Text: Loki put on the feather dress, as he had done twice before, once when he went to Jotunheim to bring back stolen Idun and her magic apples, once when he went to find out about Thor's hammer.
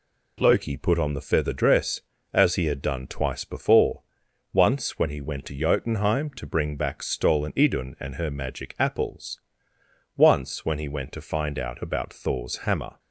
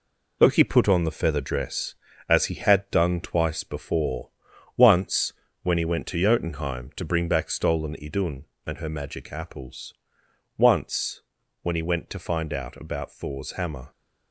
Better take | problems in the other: first | gets quieter; throughout; 6.5 dB // pauses between "once" and "when"; slight; at 5.3 s; 0.30 s long // pauses between "once" and "when"; at 11.2 s; 0.42 s long

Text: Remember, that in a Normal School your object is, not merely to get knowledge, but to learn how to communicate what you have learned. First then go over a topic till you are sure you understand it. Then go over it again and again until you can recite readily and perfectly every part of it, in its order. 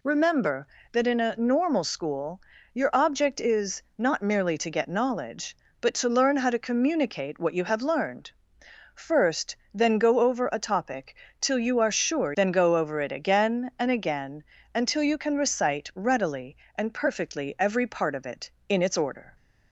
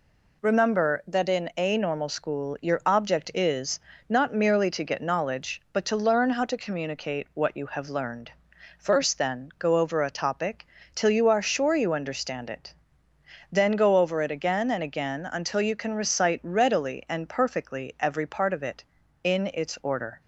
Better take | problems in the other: second | pauses between "School" and "your"; slight; at 2.4 s; 0.32 s long // pauses between "First" and "then"; slight; at 9.5 s; 0.18 s long // pauses between "topic" and "till"; slight; at 11.1 s; 0.24 s long; slight in the second // skips "you understand it"; at 12.3 s // pauses between "again" and "until"; slight; at 14.4 s; 0.32 s long

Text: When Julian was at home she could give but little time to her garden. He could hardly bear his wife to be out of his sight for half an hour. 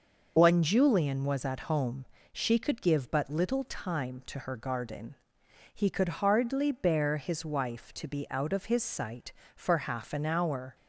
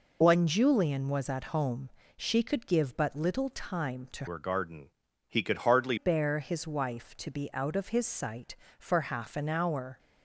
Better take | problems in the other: first | pauses between "home" and "she"; slight; at 1.8 s; 0.26 s long; slight in the first // changes voice from "her" to "hardly"; from 4.2 to 5.9 s; 1.7 s long

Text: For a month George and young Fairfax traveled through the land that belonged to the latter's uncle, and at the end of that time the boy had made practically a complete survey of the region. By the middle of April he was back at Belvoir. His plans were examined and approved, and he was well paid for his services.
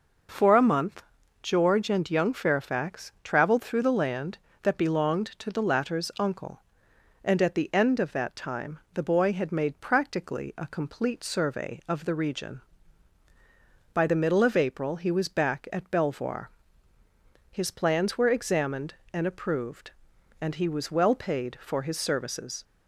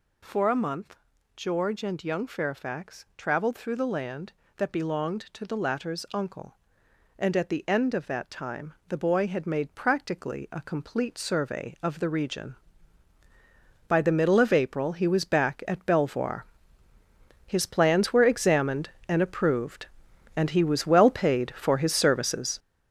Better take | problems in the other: first | gets louder; strong; throughout; 7.5 dB // pauses between "month" and "George"; at 0.9 s; 0.40 s long; also in the first

